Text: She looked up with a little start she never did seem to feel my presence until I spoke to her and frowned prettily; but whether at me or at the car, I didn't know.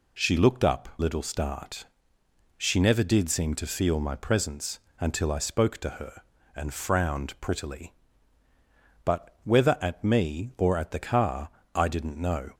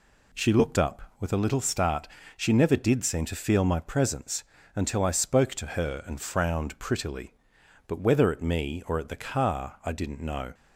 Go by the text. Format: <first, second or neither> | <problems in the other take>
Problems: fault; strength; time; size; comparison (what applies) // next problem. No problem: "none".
second | skips "with a"; at 0.9 s // pauses between "start" and "she"; noticeable; at 1.8 s; 0.72 s long; slight in the second // pauses between "presence" and "until"; slight; at 4.7 s; 0.22 s long; slight in the second